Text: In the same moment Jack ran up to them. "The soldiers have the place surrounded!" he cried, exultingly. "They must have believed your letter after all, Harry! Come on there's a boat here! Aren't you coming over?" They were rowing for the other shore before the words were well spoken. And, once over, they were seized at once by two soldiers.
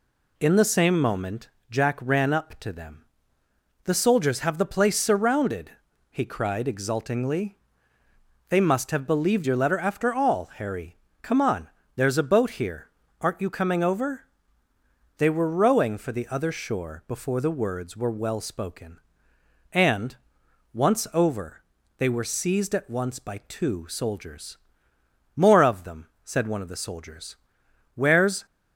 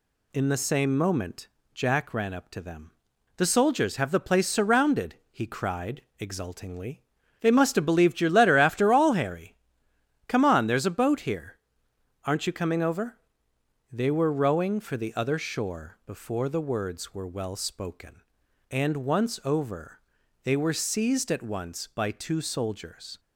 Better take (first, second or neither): second